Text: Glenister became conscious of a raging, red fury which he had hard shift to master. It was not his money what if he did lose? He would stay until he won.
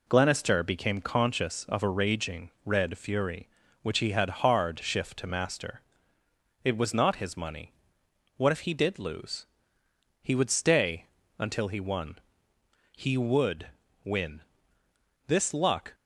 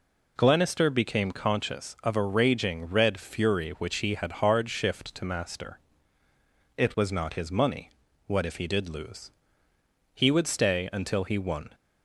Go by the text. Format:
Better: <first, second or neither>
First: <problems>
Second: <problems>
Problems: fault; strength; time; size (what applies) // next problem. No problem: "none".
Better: second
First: pauses between "money" and "what"; noticeable; at 7.7 s; 0.64 s long // pauses between "stay" and "until"; slight; at 11.0 s; 0.32 s long // goes on to say "He would win This luck"; strong; from 12.9 s on; 3.0 s long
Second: pauses between "money" and "what"; at 7.8 s; 0.38 s long